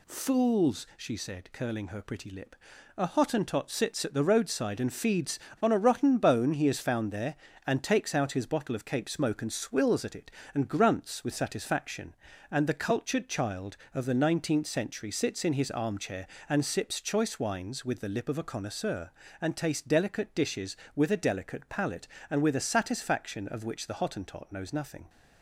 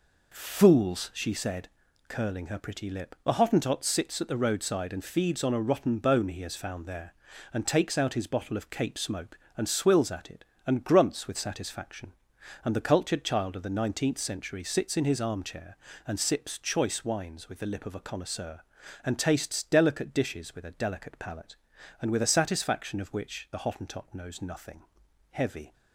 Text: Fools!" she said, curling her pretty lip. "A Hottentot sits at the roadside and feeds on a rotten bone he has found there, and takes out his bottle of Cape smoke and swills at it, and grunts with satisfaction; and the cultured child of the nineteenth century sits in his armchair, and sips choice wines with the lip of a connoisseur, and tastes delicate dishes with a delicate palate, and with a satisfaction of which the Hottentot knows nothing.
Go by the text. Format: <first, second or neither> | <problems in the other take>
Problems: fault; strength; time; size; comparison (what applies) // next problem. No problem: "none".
first | goes on to say "Heavy"; slight; from 25.3 s on; 0.42 s long